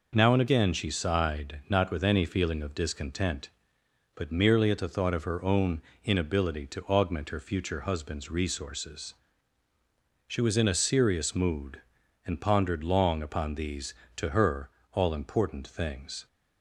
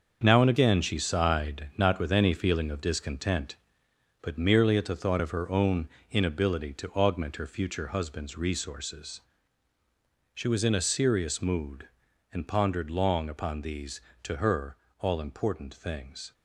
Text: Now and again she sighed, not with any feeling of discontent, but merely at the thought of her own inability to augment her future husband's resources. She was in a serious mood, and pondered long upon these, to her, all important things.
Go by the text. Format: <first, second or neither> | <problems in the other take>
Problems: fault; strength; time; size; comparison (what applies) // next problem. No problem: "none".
first | gets quieter; strong; throughout; 9 dB // pauses between "own" and "inability"; slight; at 5.8 s; 0.24 s long; slight in the first